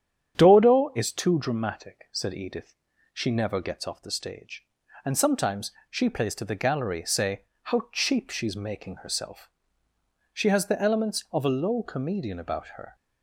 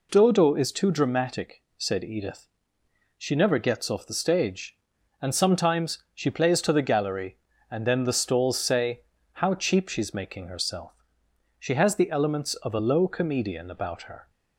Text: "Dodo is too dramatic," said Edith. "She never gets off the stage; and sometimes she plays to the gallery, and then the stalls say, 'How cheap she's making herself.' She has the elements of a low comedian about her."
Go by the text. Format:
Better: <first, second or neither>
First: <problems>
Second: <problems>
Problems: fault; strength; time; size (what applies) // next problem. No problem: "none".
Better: second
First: starts louder than the rest; strong; until 1.3 s; 9 dB // pauses between "sometimes" and "she"; slight; at 5.7 s; 0.19 s long // skips "and then the stalls"; at 7.0 s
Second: none